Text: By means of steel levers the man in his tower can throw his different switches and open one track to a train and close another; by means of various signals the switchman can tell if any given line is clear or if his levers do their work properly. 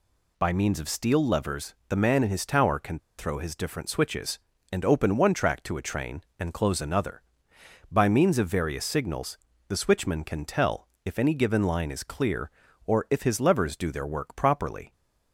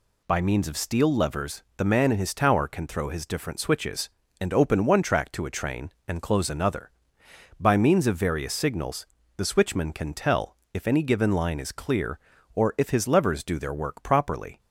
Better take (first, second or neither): second